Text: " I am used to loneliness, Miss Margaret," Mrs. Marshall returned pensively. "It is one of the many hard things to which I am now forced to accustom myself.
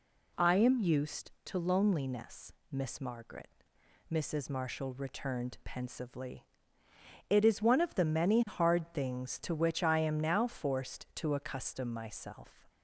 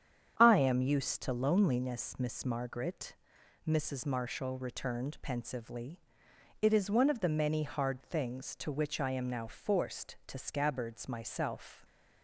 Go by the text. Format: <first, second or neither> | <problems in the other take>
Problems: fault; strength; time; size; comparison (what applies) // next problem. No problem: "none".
first | starts louder than the rest; strong; until 1.3 s; 8.5 dB // says "scabbards" for "accustom"; at 10.3 s